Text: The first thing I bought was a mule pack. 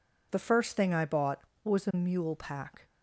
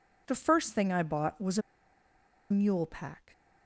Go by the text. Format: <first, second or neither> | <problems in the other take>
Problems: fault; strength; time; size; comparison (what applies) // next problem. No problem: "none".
first | pauses between "a" and "mule"; noticeable; at 1.6 s; 0.90 s long